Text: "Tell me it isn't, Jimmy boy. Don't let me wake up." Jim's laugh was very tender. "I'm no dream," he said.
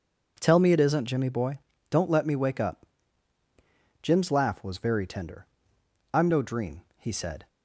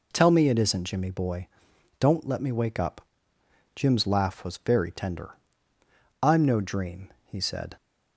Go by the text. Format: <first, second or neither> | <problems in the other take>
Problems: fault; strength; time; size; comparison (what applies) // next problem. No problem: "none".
neither | none